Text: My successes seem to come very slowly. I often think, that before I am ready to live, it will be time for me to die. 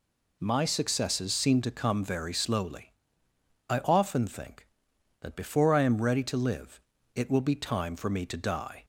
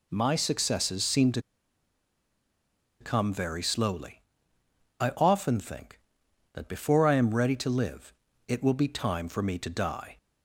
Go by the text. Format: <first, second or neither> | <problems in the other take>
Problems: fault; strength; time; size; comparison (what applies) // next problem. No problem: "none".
first | pauses between "to" and "come"; strong; at 1.4 s; 1.5 s long